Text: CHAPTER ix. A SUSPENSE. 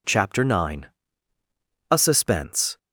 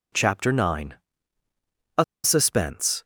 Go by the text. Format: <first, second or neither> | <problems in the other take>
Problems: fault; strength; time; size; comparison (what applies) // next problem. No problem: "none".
first | pauses between "A" and "SUSPENSE"; slight; at 2.0 s; 0.19 s long